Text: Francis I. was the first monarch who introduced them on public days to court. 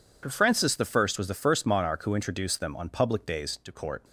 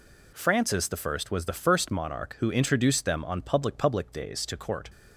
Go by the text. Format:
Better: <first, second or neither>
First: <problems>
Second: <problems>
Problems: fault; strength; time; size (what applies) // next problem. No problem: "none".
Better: first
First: none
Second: says "public" twice; at 3.7 s